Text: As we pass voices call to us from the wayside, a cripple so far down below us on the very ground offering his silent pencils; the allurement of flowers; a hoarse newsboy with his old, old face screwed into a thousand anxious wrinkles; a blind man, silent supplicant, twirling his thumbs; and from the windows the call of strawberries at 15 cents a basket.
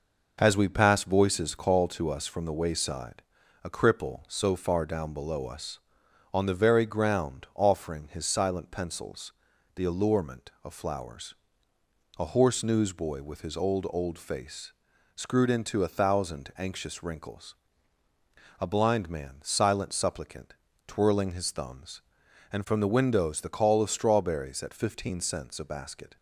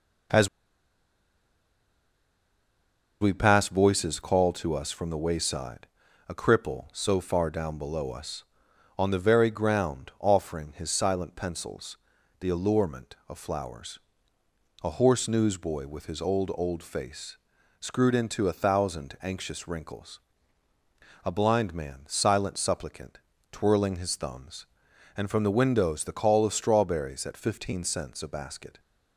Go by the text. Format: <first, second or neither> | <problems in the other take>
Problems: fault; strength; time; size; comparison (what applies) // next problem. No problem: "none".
first | pauses between "As" and "we"; strong; at 0.4 s; 2.7 s long // pauses between "face" and "screwed"; noticeable; at 17.3 s; 0.46 s long; noticeable in the first